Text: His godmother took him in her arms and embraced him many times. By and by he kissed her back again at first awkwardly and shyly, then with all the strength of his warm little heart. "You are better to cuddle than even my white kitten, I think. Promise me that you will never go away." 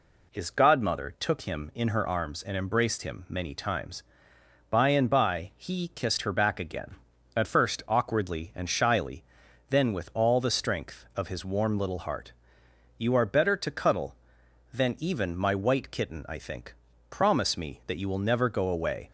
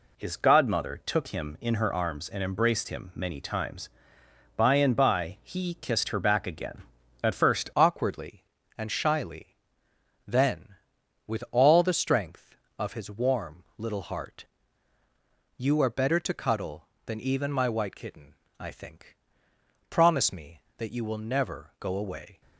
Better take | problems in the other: first | changes voice at "awkwardly"; from 7.7 s on; 14.7 s long

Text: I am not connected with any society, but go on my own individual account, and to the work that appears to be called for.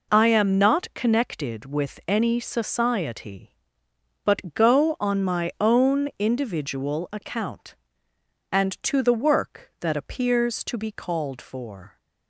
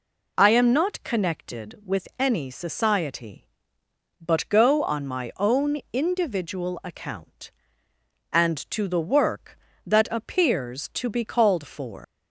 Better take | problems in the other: first | leaves "for" unfinished; at 12.0 s; 120 ms

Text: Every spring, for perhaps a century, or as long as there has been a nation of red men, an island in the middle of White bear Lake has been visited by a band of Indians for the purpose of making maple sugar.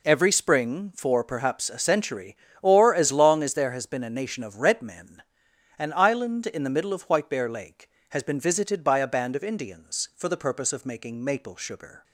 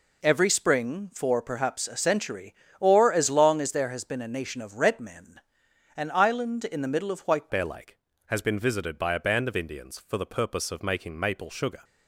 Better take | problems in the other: first | changes voice at "bear"; from 7.5 s on; 4.3 s long

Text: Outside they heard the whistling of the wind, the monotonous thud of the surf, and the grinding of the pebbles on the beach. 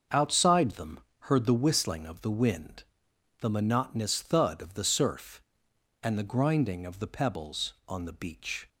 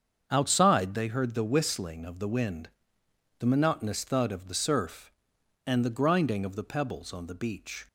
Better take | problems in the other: second | starts louder than the rest; until 1.3 s; 6.5 dB; also in the second // says "them" for "they"; at 0.7 s

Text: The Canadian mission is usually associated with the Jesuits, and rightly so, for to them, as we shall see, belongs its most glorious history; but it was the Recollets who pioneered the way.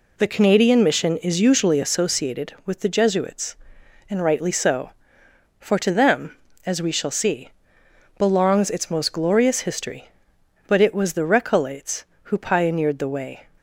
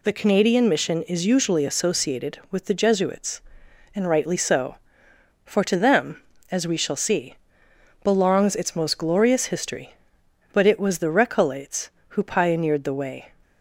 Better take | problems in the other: second | starts louder than the rest; slight; until 2.1 s; 2.5 dB

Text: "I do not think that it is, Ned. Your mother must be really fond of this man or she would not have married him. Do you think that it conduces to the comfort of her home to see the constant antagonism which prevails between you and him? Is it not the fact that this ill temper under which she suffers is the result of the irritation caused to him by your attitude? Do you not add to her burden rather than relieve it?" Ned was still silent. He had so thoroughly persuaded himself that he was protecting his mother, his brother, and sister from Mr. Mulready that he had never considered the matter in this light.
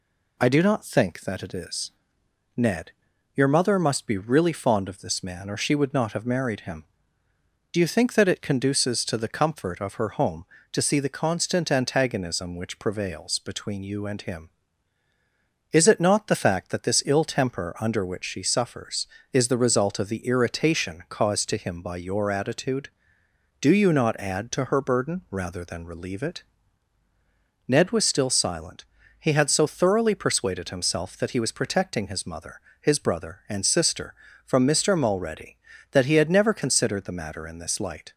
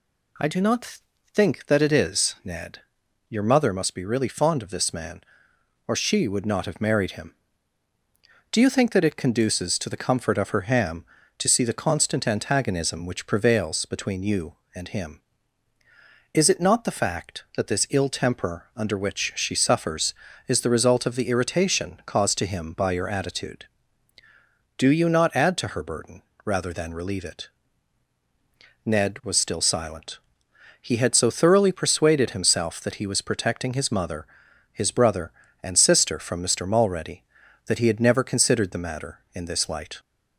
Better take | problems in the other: first | pauses between "not" and "think"; slight; at 0.9 s; 0.34 s long // says "ham" for "home"; at 10.6 s // pauses between "burden" and "rather"; slight; at 26.2 s; 0.24 s long

